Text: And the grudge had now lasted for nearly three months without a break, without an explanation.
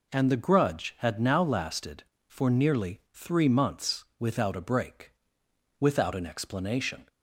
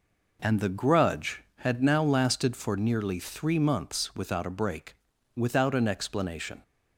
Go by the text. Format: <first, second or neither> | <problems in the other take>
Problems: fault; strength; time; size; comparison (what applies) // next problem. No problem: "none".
neither | none